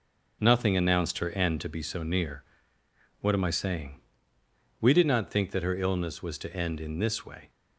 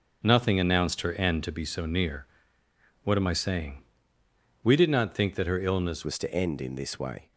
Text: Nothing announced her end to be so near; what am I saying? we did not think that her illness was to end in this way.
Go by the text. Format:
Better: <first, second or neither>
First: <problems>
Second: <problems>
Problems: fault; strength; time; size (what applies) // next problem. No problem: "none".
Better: first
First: none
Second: changes voice at "was"; from 6.0 s on; 1.3 s long